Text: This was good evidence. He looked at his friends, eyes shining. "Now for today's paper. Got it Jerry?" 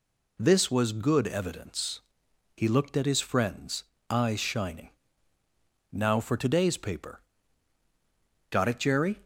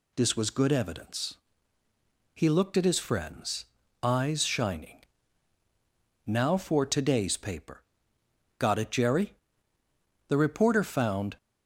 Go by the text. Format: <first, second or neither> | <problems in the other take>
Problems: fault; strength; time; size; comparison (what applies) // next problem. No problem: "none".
first | goes on to say "The reporter found"; noticeable; from 10.2 s on; 1.1 s long